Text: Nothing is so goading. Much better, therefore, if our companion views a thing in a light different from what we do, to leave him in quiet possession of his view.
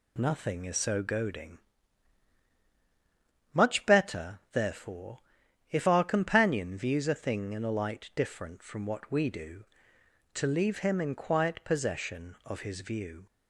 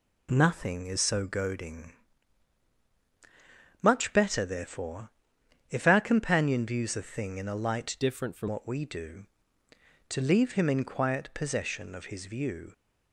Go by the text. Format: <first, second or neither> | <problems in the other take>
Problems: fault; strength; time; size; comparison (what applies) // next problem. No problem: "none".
first | changes voice from "different" to "from"; from 8.0 to 8.4 s; 0.4 s long